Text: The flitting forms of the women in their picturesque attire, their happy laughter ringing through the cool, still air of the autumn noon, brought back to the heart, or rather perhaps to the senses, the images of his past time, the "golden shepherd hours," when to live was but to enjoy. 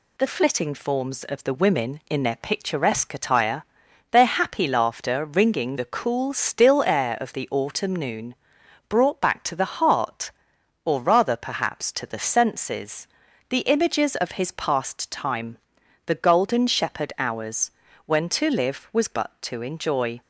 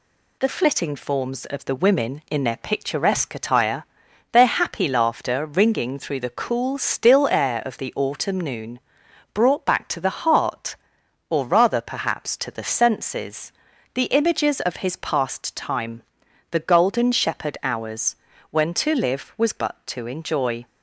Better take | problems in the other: second | skips "through"; at 5.7 s

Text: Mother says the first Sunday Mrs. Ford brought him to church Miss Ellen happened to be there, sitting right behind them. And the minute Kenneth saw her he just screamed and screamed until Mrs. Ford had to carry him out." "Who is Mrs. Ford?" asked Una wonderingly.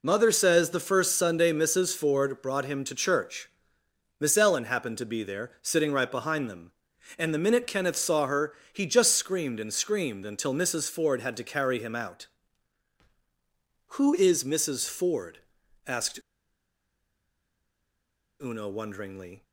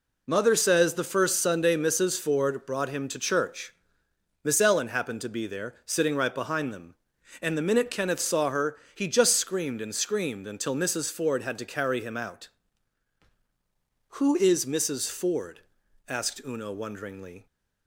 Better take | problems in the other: second | pauses between "church" and "Miss"; noticeable; at 3.4 s; 0.72 s long; noticeable in the second // pauses between "her" and "he"; slight; at 8.5 s; 0.20 s long; slight in the second // pauses between "asked" and "Una"; strong; at 16.2 s; 2.2 s long

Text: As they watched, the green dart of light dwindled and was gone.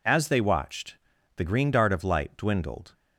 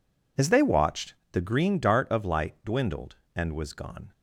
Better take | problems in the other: second | stops before "and was gone"; at 2.9 s

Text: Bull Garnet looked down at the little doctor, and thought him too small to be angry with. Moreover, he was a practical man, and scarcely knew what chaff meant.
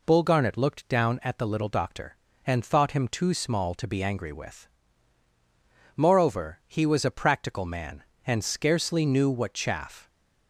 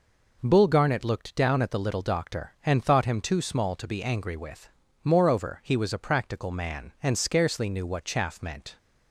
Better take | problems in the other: second | stops before "meant"; at 10.0 s

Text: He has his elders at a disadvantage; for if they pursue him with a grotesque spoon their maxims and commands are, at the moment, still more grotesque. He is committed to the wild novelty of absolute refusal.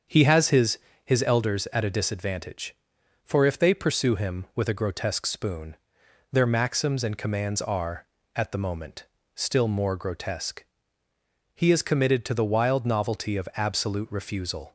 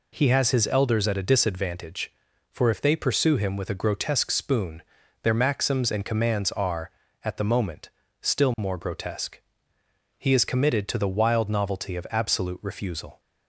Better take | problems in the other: second | starts louder than the rest; until 1.4 s; 7 dB // says "his" twice; at 1.0 s // pauses between "spoon" and "their"; noticeable; at 5.7 s; 0.56 s long; also in the second

